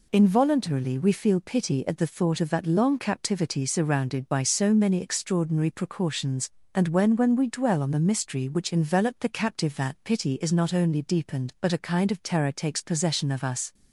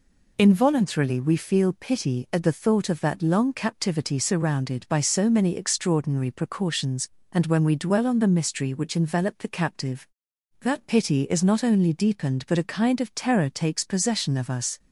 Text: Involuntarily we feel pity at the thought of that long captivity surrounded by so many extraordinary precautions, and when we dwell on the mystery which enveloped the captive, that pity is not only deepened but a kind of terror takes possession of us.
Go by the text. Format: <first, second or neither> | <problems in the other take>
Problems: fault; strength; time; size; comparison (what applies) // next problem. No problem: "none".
second | says "when" twice; at 7.1 s